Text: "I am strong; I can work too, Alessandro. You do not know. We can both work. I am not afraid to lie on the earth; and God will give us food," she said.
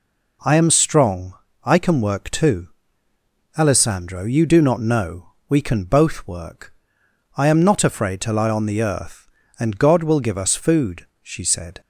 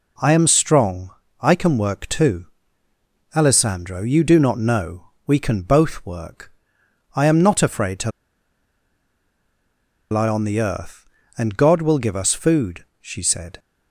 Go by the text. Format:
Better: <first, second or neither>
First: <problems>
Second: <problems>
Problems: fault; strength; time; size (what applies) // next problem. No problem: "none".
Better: first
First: none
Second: pauses between "to" and "lie"; strong; at 8.1 s; 2.0 s long